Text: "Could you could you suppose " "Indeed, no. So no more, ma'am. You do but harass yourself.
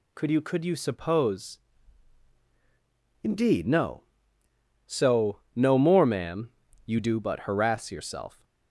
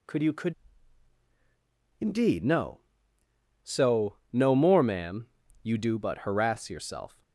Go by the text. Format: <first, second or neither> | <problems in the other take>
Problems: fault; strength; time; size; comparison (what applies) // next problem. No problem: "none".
first | skips "you suppose"; at 0.8 s // pauses between "So" and "no"; slight; at 4.1 s; 0.16 s long; slight in the first